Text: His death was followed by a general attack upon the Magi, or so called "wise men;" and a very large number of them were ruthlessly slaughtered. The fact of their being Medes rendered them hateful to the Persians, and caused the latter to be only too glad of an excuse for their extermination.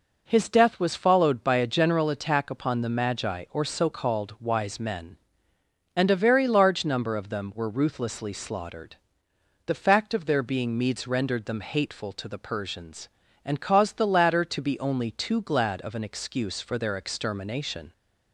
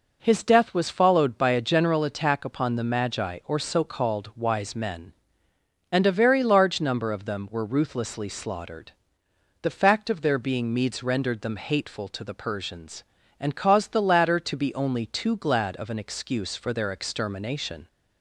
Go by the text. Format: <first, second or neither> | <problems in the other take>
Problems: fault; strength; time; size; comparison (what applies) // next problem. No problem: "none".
neither | none